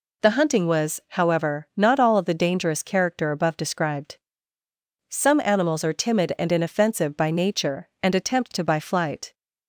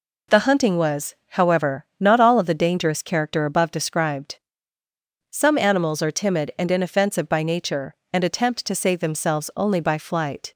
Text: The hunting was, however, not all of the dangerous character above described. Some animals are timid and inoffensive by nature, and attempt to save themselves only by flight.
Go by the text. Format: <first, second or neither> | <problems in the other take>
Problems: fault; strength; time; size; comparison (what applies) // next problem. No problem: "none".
second | skips "save themselves only"; at 8.6 s